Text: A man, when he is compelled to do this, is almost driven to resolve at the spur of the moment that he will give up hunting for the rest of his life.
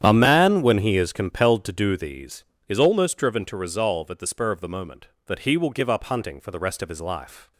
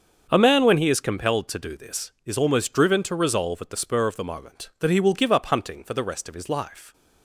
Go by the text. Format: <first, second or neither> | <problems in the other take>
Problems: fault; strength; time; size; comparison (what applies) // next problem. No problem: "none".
second | starts louder than the rest; strong; until 1.0 s; 9.5 dB; also in the second // says "these" for "this"; at 1.9 s